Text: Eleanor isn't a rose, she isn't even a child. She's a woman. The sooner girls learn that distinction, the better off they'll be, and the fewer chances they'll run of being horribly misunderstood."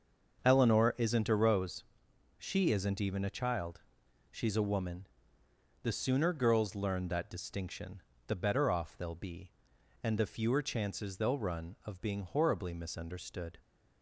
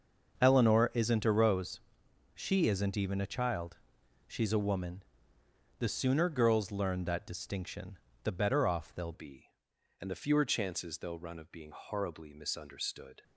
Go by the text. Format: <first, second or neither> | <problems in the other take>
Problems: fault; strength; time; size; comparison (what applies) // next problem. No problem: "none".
first | starts louder than the rest; until 1.4 s; 6.5 dB; also in the first // changes voice at "be"; from 9.1 s on; 4.1 s long